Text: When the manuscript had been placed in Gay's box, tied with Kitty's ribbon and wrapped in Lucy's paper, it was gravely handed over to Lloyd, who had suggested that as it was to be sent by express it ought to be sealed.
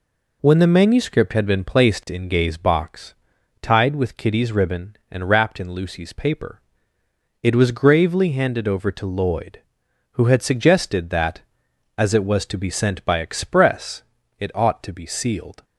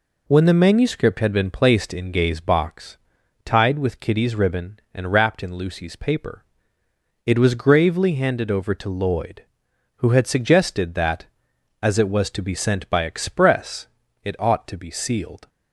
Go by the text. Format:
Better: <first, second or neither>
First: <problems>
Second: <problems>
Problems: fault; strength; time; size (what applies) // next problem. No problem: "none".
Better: neither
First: pauses between "express" and "it"; slight; at 14.0 s; 0.36 s long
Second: pauses between "express" and "it"; slight; at 13.8 s; 0.36 s long